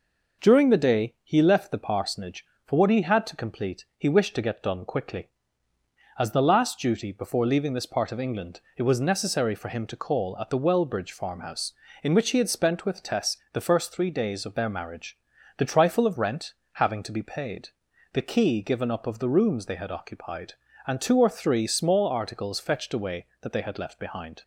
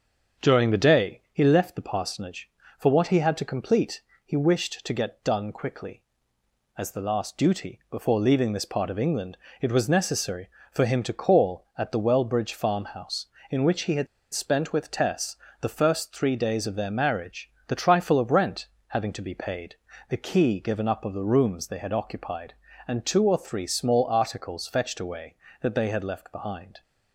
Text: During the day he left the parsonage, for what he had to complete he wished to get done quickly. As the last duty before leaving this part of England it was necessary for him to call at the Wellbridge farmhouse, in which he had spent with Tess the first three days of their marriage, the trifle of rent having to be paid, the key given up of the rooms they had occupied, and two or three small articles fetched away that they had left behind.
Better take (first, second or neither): first